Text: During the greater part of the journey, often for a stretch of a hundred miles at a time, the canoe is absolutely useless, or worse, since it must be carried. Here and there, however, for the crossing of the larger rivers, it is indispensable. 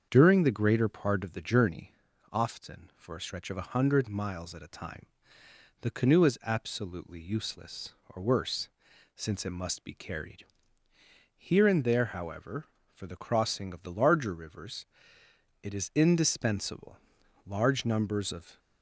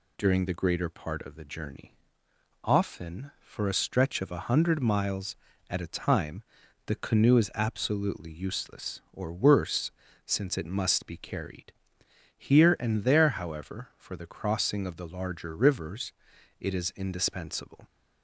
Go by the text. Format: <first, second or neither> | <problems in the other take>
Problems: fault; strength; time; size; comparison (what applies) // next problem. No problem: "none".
second | starts louder than the rest; strong; until 1.1 s; 7 dB // goes on to say "Large numbers of"; noticeable; from 17.4 s on; 1.1 s long